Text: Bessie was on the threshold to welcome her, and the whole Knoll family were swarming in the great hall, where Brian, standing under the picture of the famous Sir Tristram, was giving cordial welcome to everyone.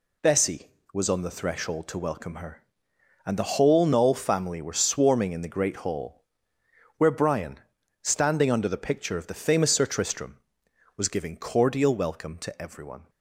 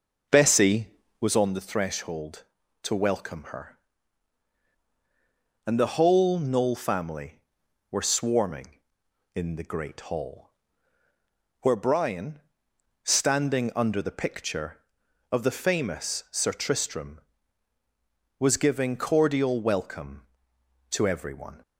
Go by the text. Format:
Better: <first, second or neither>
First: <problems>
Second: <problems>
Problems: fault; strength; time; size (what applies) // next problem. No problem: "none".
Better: first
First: none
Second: starts louder than the rest; noticeable; until 1.4 s; 5.5 dB